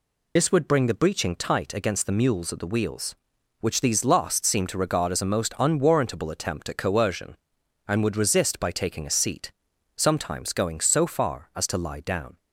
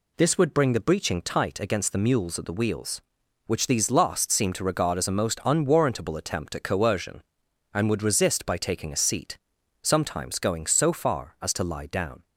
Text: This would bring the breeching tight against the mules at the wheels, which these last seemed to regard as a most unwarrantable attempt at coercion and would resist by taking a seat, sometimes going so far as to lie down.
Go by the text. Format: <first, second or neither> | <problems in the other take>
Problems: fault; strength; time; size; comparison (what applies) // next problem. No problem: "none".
second | loses the start of "This"; at 0.3 s; 55 ms